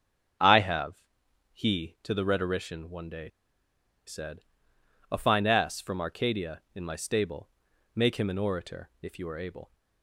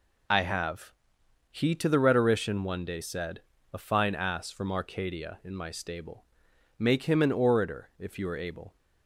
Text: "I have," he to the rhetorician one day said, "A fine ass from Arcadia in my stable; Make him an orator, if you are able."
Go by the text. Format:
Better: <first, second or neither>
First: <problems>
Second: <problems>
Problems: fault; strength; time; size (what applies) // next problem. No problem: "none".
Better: second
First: starts louder than the rest; strong; until 1.9 s; 8 dB // pauses between "day" and "said"; noticeable; at 3.2 s; 0.78 s long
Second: none